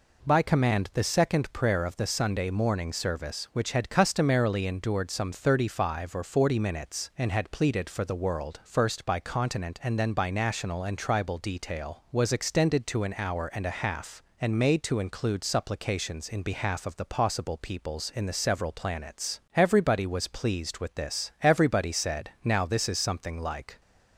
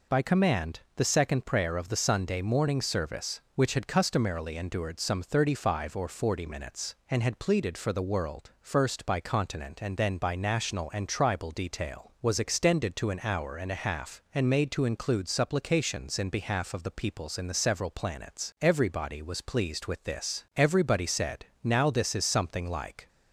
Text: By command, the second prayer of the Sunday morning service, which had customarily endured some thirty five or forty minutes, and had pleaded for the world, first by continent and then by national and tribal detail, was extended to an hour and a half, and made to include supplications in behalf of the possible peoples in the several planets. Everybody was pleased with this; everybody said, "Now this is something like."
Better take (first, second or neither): first